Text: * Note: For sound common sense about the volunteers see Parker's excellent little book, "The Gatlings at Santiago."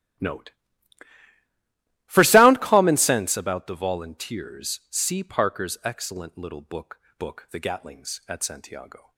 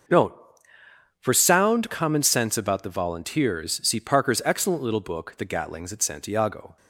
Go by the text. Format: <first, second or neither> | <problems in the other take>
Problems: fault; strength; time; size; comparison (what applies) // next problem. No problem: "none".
second | starts louder than the rest; strong; until 2.7 s; 14 dB; noticeable in the second // says "book" twice; at 7.1 s